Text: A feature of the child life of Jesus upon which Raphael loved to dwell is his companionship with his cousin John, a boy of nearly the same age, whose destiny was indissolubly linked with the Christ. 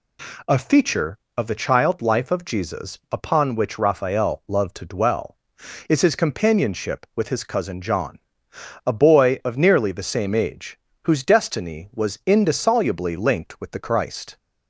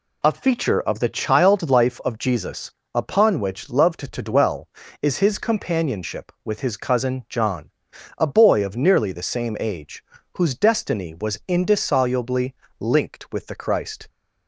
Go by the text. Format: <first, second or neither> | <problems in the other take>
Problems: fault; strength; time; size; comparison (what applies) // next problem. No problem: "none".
first | pauses between "Jesus" and "upon"; slight; at 2.7 s; 0.20 s long // skips "Raphael"; at 3.6 s // pauses between "indissolubly" and "linked"; slight; at 12.5 s; 0.24 s long